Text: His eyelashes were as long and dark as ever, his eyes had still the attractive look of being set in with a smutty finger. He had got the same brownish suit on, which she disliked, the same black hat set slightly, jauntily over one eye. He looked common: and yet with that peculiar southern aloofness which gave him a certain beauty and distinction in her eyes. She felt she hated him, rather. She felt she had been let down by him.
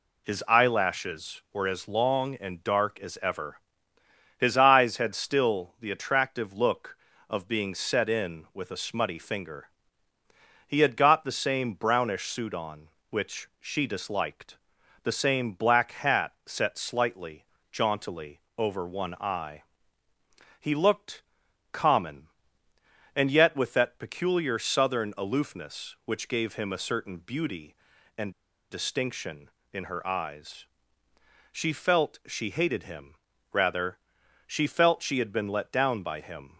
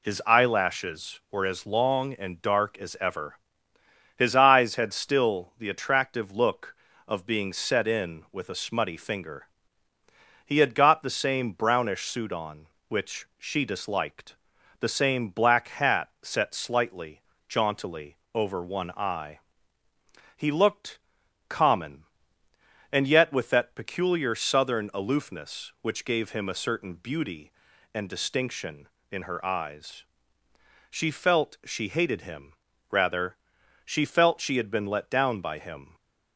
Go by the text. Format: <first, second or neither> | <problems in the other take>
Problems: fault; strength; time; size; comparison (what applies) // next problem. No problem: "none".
second | pauses between "jauntily" and "over"; slight; at 18.4 s; 0.16 s long; slight in the second // pauses between "looked" and "common"; noticeable; at 21.2 s; 0.50 s long; noticeable in the second // pauses between "and" and "distinction"; at 28.3 s; 0.38 s long